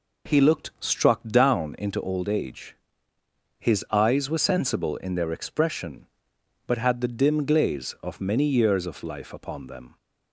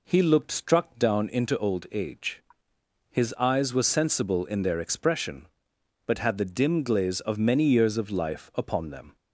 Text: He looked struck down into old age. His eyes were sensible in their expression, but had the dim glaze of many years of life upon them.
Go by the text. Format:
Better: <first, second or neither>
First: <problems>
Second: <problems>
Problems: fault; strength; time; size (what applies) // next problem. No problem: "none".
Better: neither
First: none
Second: none